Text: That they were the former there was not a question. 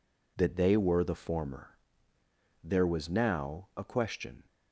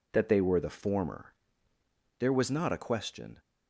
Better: second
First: pauses between "former" and "there"; noticeable; at 1.7 s; 0.96 s long // says "now" for "not"; at 3.1 s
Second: pauses between "former" and "there"; noticeable; at 1.3 s; 0.84 s long

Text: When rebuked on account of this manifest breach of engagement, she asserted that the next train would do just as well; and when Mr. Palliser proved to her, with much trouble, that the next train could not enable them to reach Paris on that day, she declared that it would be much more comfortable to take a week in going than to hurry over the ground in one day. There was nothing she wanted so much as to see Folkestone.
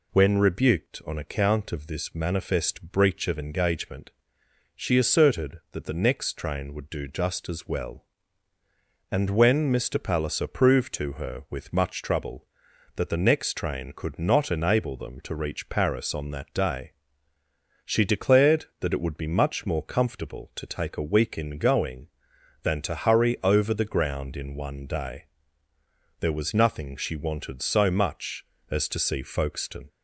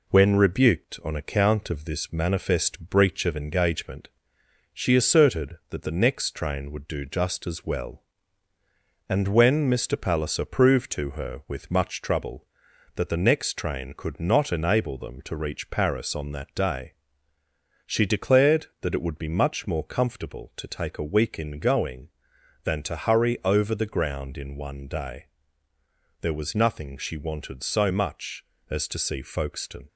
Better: first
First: none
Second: gets quieter; slight; throughout; 2 dB

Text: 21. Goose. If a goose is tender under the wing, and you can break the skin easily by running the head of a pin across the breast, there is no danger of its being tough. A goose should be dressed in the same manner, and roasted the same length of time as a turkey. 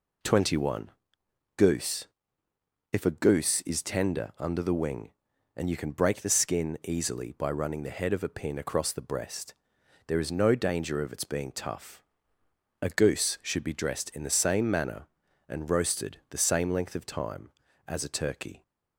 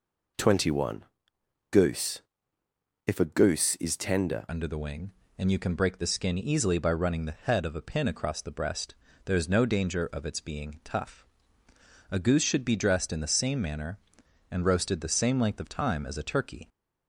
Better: first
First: none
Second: changes voice at "under"; from 4.4 s on; 12.2 s long

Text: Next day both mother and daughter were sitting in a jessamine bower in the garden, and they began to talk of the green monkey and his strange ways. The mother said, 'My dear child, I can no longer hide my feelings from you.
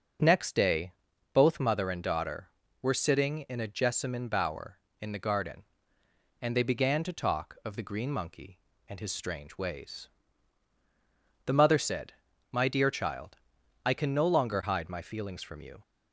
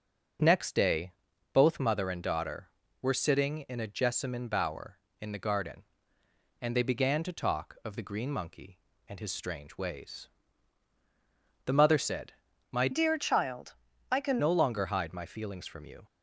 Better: first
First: pauses between "day" and "both"; at 0.9 s; 0.40 s long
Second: pauses between "day" and "both"; at 1.1 s; 0.40 s long // changes voice from "dear" to "can"; from 12.9 to 14.3 s; 1.4 s long

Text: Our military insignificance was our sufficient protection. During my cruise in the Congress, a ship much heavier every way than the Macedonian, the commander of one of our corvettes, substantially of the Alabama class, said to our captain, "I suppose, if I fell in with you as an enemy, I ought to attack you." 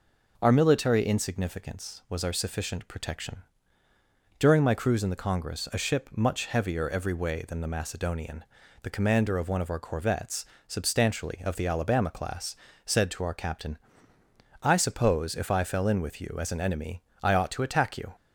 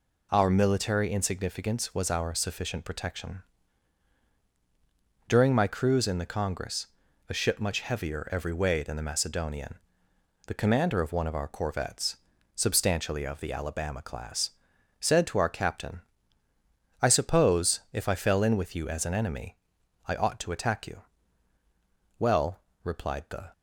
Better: first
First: none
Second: goes on to say "Well replied the"; from 22.1 s on; 1.3 s long

